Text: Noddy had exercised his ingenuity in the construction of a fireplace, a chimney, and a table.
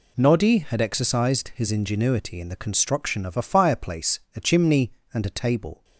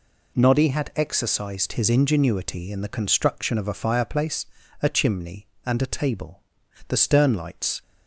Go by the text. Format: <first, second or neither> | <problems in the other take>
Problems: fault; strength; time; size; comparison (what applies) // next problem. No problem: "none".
first | goes on to say "The stern lights"; noticeable; from 6.8 s on; 0.94 s long